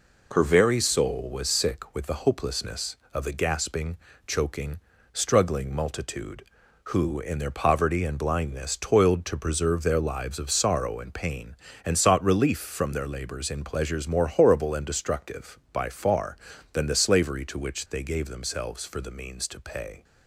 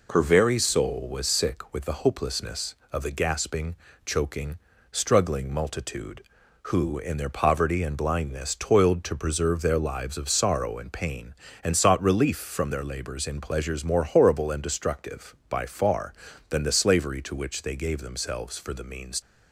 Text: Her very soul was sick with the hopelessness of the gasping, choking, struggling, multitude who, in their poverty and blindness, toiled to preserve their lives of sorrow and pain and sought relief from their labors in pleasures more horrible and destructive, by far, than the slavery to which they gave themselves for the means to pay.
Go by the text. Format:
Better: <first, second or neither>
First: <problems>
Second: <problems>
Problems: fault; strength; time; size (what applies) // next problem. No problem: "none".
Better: first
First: none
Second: stops before "to pay"; at 19.2 s